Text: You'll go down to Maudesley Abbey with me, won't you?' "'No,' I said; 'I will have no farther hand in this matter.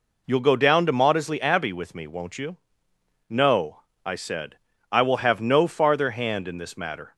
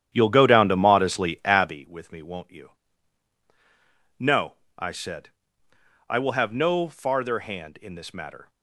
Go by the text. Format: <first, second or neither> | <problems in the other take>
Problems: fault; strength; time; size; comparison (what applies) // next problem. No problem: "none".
first | starts louder than the rest; strong; until 1.8 s; 10 dB